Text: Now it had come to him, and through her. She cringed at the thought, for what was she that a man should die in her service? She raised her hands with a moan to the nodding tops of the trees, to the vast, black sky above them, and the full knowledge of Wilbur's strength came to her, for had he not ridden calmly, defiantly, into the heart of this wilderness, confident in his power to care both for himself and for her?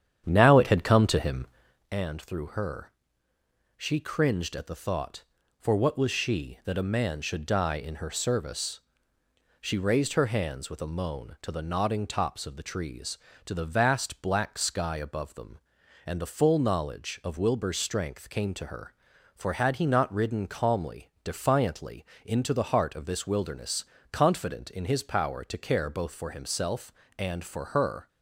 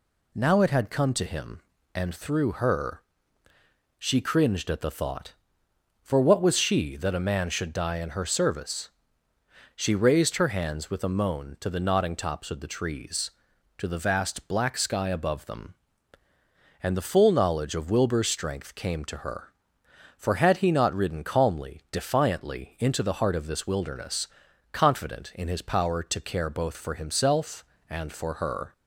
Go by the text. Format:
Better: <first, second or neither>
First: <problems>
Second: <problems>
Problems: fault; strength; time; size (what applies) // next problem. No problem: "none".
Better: second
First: starts louder than the rest; strong; until 1.9 s; 9.5 dB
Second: none